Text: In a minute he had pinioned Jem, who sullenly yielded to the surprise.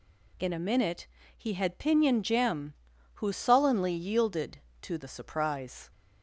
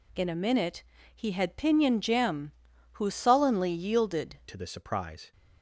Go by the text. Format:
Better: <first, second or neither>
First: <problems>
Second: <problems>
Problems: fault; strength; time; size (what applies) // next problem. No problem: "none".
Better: first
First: pauses between "minute" and "he"; slight; at 1.0 s; 0.30 s long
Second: pauses between "minute" and "he"; slight; at 0.8 s; 0.32 s long // changes voice at "to"; from 4.4 s on; 0.9 s long